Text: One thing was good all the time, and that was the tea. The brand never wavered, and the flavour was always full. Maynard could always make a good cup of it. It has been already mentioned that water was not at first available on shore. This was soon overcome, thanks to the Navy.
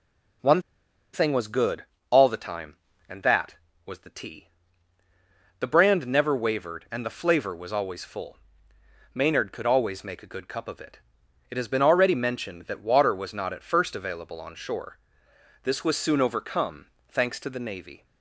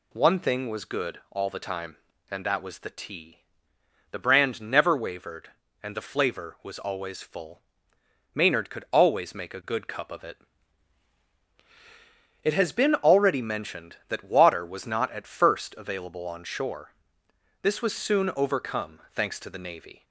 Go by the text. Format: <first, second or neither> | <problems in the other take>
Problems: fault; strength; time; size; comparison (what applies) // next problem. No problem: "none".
second | pauses between "One" and "thing"; noticeable; at 0.6 s; 0.51 s long // pauses between "good" and "all"; slight; at 1.8 s; 0.26 s long